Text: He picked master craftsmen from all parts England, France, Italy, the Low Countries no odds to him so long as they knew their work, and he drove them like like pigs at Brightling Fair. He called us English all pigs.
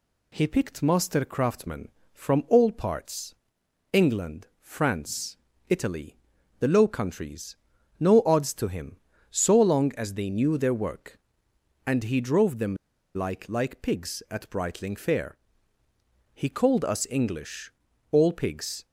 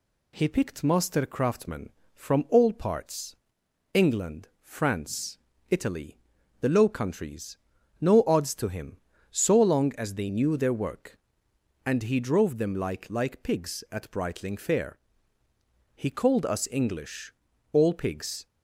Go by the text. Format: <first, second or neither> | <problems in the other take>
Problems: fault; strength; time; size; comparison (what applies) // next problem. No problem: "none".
second | pauses between "parts" and "England"; noticeable; at 3.3 s; 0.56 s long; noticeable in the second // pauses between "Countries" and "no"; at 7.5 s; 0.44 s long; also in the second // pauses between "them" and "like"; at 12.7 s; 0.39 s long // pauses between "English" and "all"; at 17.6 s; 0.40 s long; also in the second